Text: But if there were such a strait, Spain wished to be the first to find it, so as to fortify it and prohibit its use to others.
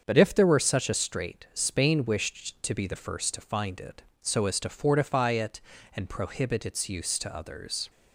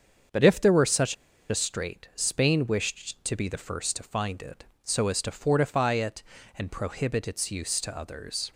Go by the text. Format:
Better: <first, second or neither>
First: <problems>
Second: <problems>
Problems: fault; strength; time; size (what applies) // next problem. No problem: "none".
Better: first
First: starts louder than the rest; until 1.0 s; 7 dB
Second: starts louder than the rest; until 1.6 s; 7 dB // pauses between "such" and "a"; slight; at 1.1 s; 0.35 s long